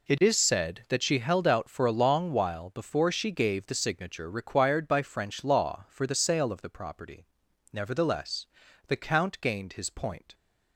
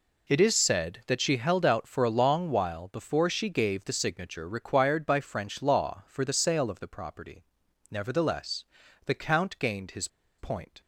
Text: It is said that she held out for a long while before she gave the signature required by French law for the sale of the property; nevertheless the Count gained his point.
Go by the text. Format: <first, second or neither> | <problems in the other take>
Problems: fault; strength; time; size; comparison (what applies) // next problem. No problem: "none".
first | pauses between "nevertheless" and "the"; at 8.6 s; 0.40 s long; also in the first // pauses between "his" and "point"; slight; at 10.0 s; 0.30 s long